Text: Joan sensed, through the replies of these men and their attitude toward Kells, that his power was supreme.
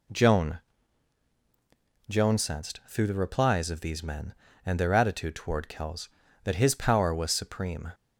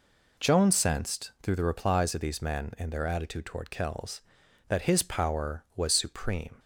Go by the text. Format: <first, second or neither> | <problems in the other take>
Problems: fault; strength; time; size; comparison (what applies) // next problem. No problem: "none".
second | says "Joan" twice; at 2.0 s